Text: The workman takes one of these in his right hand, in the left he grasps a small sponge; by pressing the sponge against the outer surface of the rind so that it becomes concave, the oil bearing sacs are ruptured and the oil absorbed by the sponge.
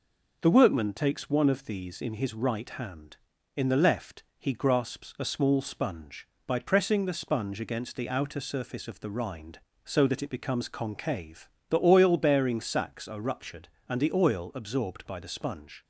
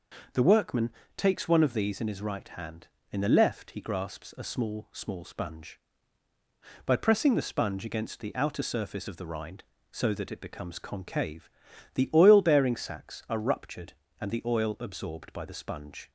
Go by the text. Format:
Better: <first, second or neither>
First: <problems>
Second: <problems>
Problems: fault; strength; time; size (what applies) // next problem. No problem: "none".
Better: first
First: none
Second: pauses between "workman" and "takes"; slight; at 0.9 s; 0.26 s long // says "small" twice; at 4.9 s